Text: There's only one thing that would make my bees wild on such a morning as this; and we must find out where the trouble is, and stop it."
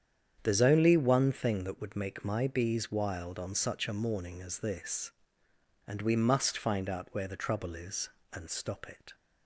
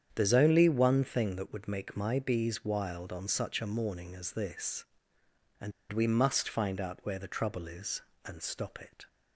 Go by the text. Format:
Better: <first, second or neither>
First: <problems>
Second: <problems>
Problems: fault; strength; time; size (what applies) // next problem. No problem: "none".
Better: first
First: starts louder than the rest; strong; until 1.4 s; 8.5 dB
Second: starts louder than the rest; strong; until 1.1 s; 8.5 dB // pauses between "and" and "we"; slight; at 5.7 s; 0.19 s long